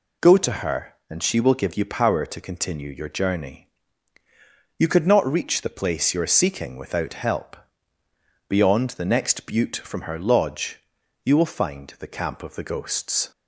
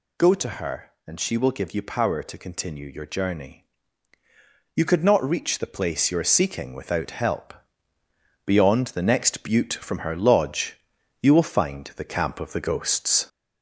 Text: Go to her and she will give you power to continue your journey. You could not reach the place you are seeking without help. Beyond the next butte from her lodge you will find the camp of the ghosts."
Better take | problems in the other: first | gets louder; noticeable; throughout; 4 dB // pauses between "lodge" and "you"; at 10.7 s; 0.44 s long; also in the first

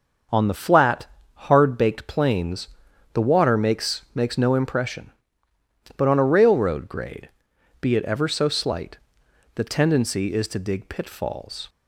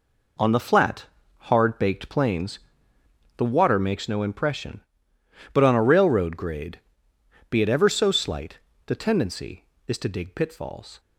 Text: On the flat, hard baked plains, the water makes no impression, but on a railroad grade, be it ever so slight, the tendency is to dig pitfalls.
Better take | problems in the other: second | starts louder than the rest; until 1.5 s; 6 dB // says "makes" twice; at 4.1 s

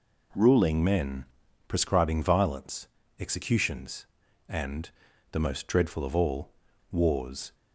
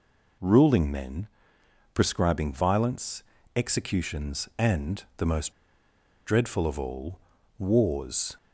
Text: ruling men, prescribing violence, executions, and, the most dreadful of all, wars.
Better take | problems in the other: first | pauses between "most" and "dreadful"; noticeable; at 5.5 s; 0.74 s long

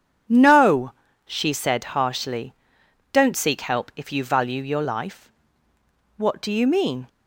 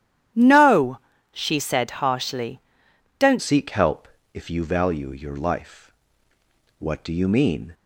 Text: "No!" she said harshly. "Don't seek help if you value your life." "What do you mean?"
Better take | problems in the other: first | starts louder than the rest; strong; until 1.6 s; 11 dB // changes voice at "seek"; from 3.4 s on; 4.3 s long // pauses between "help" and "if"; slight; at 4.0 s; 0.26 s long

